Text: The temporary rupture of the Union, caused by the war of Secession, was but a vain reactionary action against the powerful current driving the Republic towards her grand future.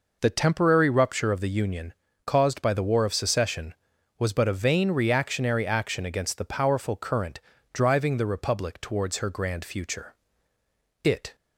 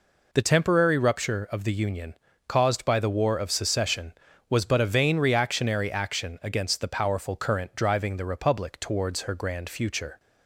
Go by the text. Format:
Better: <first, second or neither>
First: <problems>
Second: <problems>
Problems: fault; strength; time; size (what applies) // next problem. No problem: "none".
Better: second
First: pauses between "current" and "driving"; slight; at 7.3 s; 0.32 s long // goes on to say "It"; slight; from 11.0 s on; 0.30 s long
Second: none